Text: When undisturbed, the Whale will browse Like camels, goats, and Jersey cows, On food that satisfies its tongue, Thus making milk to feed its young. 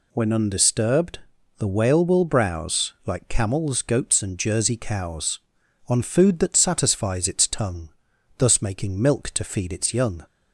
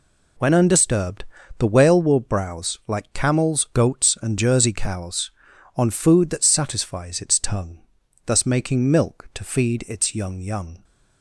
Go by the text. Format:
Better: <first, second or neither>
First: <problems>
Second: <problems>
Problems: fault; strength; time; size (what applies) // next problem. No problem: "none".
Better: first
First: none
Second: says "young" twice; at 10.3 s